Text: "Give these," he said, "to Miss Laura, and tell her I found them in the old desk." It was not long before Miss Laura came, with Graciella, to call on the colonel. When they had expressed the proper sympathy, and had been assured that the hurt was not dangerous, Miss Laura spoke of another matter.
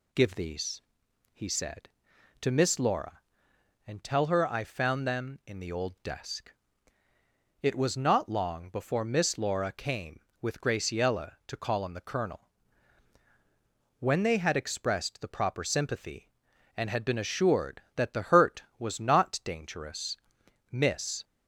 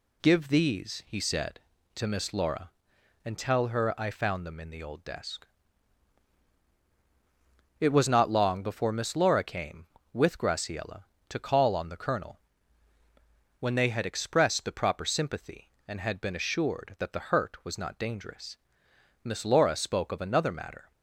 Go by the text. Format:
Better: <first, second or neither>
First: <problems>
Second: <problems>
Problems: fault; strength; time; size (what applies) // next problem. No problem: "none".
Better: second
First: stops before "Laura spoke of another matter"; at 21.2 s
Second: none